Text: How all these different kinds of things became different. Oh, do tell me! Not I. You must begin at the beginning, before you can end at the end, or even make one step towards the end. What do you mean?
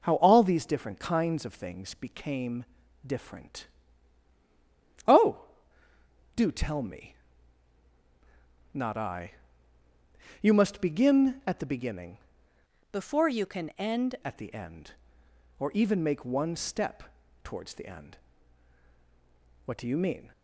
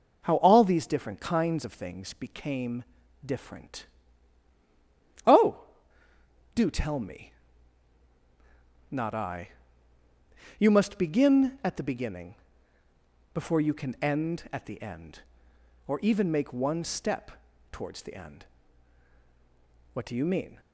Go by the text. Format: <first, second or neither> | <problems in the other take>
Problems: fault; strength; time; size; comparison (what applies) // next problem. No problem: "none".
second | pauses between "became" and "different"; at 2.6 s; 0.42 s long; also in the second // changes voice from "before" to "end"; from 12.9 to 14.1 s; 1.2 s long // pauses between "step" and "towards"; at 17.0 s; 0.40 s long; also in the second